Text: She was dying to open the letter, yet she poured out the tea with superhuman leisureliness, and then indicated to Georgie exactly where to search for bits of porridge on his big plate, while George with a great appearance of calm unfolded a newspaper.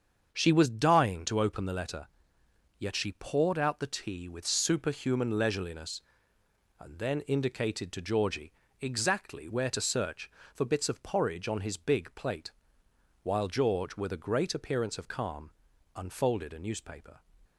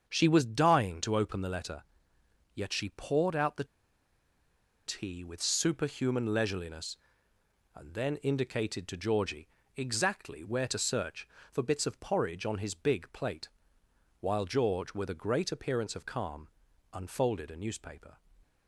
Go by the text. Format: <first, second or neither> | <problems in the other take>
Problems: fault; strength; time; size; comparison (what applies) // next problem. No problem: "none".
first | starts louder than the rest; until 1.0 s; 7 dB; also in the first // pauses between "the" and "tea"; at 3.6 s; 1.2 s long // pauses between "Georgie" and "exactly"; slight; at 9.4 s; 0.26 s long; slight in the first // pauses between "calm" and "unfolded"; at 16.4 s; 0.44 s long; also in the first